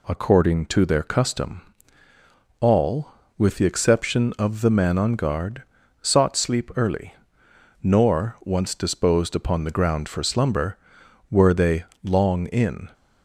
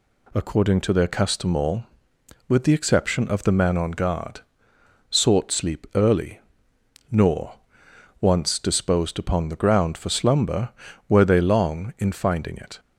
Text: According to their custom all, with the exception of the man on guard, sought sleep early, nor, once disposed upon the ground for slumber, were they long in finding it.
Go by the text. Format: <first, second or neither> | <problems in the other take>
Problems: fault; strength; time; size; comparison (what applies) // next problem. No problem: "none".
second | pauses between "custom" and "all"; at 1.6 s; 1.0 s long // pauses between "they" and "long"; slight; at 11.8 s; 0.18 s long // stops before "finding it"; at 12.9 s